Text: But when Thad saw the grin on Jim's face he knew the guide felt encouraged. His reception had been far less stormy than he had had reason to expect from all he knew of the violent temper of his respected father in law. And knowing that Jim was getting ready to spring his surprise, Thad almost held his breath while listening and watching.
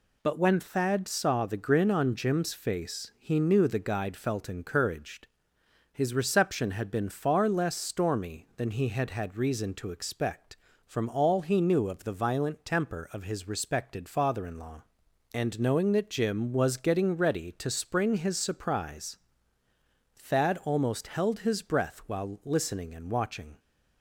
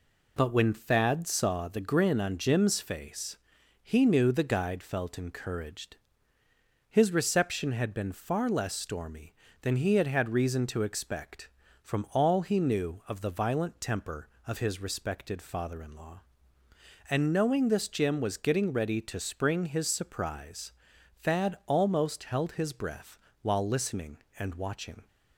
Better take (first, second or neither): first